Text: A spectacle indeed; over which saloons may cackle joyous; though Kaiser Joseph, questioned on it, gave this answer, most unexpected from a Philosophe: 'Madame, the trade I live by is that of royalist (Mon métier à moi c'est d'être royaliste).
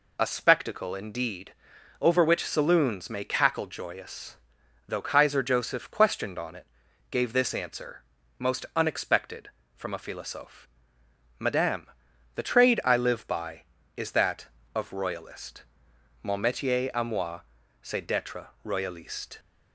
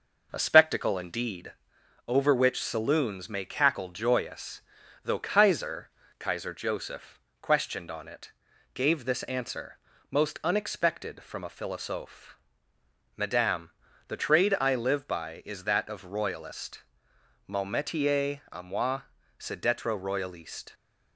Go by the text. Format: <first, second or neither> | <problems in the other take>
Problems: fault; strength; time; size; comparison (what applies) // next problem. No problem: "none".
first | says "Kaiser" twice; at 6.1 s // pauses between "moi" and "c'est"; slight; at 19.0 s; 0.34 s long; also in the first